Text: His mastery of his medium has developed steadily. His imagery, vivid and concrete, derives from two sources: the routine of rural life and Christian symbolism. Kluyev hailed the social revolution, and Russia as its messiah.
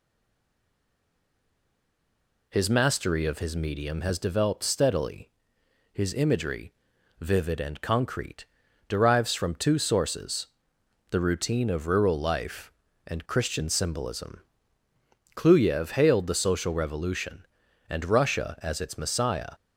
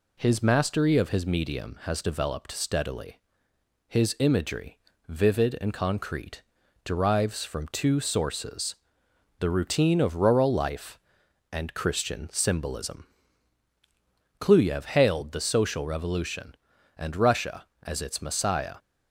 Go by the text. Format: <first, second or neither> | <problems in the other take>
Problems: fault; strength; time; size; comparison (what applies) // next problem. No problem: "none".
second | stays silent before the first word; until 2.4 s; 2.4 s long